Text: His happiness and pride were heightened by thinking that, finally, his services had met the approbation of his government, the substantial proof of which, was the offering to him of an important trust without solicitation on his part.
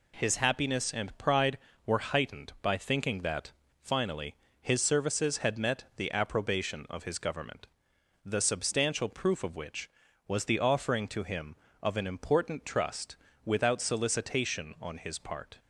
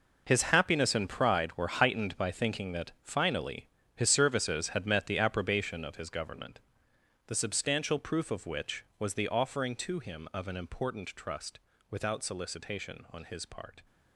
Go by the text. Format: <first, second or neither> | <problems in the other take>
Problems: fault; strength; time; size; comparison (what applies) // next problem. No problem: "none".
first | gets quieter; strong; throughout; 12.5 dB // pauses between "trust" and "without"; slight; at 11.5 s; 0.30 s long; slight in the first